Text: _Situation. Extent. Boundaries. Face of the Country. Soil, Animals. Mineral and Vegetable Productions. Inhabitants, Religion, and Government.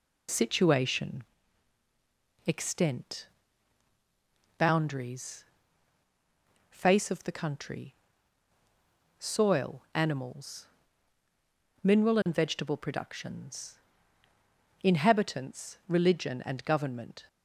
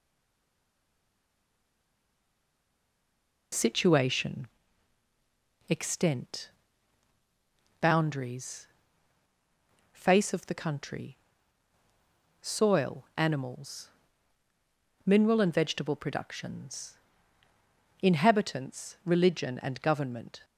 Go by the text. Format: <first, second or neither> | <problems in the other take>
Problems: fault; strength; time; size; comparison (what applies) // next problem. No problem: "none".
first | stays silent before the first word; strong; until 3.5 s; 3.5 s long